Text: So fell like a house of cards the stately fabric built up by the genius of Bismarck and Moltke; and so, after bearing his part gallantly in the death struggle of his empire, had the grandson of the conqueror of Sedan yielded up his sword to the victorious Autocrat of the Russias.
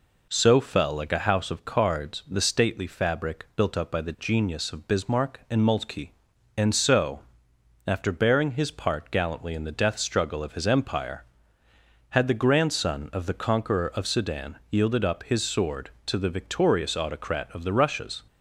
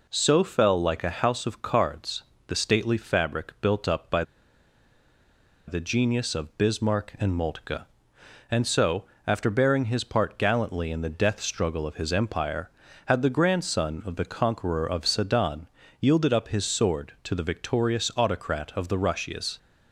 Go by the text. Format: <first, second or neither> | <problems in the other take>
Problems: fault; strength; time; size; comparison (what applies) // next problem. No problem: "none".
first | pauses between "cards" and "the"; slight; at 2.2 s; 0.24 s long // pauses between "by" and "the"; strong; at 4.2 s; 1.4 s long // pauses between "Sedan" and "yielded"; slight; at 15.6 s; 0.32 s long